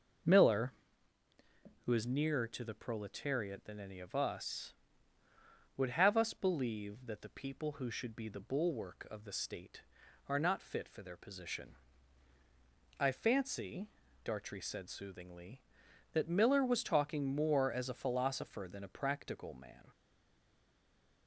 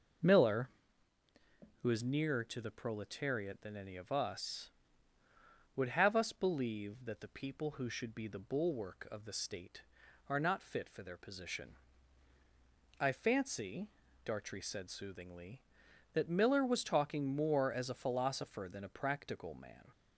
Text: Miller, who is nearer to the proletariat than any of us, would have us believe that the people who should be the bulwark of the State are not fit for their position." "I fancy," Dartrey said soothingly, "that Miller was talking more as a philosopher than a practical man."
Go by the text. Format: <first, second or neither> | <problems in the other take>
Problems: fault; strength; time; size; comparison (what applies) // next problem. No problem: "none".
second | stays silent after the last word; noticeable; from 19.9 s on; 1.3 s long